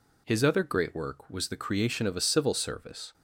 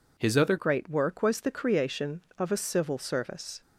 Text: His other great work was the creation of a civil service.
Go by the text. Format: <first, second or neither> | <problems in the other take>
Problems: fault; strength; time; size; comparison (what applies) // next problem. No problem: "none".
first | changes voice at "great"; from 0.5 s on; 3.1 s long